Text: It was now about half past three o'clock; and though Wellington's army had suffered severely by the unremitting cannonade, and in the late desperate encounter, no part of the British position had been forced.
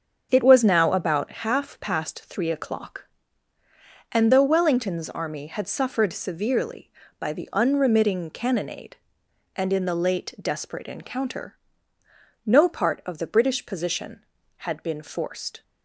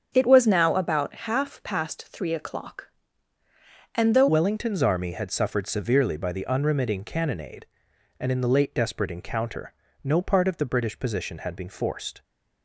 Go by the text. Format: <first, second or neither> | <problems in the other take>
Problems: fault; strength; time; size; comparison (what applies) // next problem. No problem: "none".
first | starts louder than the rest; strong; until 1.1 s; 7.5 dB; strong in the first // changes voice at "Wellington's"; from 4.2 s on; 8.0 s long